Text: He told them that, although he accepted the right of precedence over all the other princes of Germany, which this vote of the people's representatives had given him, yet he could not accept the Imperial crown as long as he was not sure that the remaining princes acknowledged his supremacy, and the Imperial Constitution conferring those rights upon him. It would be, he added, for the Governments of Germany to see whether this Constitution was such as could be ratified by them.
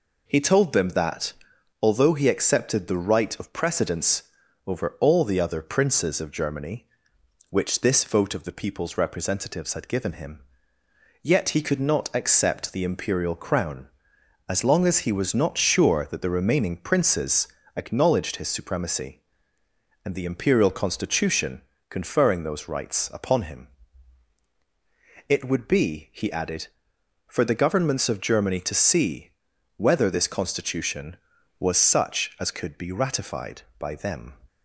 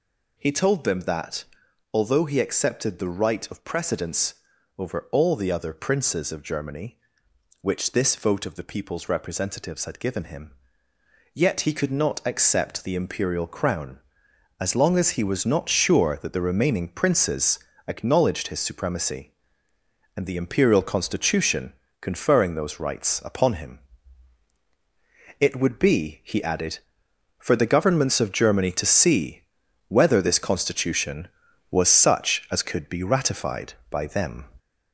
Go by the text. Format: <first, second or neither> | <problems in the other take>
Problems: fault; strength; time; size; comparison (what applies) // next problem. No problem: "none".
first | gets louder; noticeable; throughout; 4 dB // pauses between "precedence" and "over"; at 4.3 s; 0.42 s long; also in the first // pauses between "princes" and "acknowledged"; slight; at 17.5 s; 0.28 s long; slight in the first // pauses between "Constitution" and "conferring"; slight; at 21.7 s; 0.28 s long; slight in the first // pauses between "see" and "whether"; noticeable; at 29.4 s; 0.46 s long; noticeable in the first